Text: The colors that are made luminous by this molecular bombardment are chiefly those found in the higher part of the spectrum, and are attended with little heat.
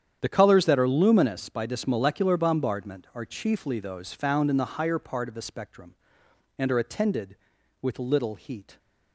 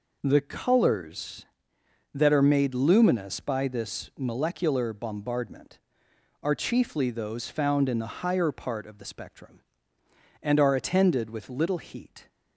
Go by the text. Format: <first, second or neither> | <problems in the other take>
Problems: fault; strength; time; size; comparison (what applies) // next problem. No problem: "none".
second | starts louder than the rest; strong; until 1.2 s; 9 dB // skips "made"; at 0.8 s